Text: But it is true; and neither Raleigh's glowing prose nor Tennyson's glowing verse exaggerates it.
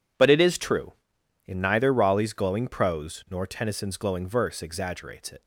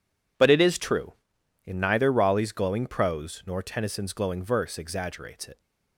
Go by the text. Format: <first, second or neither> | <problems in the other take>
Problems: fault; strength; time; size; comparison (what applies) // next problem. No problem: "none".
neither | none